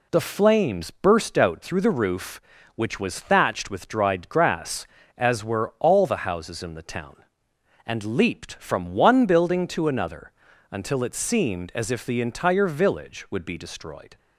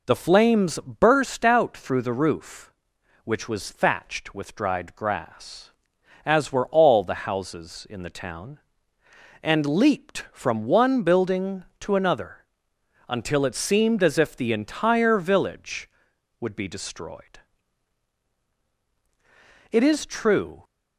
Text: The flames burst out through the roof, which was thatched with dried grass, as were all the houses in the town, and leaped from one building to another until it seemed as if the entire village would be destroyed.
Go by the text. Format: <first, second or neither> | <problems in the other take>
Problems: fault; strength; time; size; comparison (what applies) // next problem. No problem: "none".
first | pauses between "another" and "until"; noticeable; at 12.3 s; 0.70 s long; also in the first // goes on to say "It is true"; noticeable; from 19.6 s on; 0.94 s long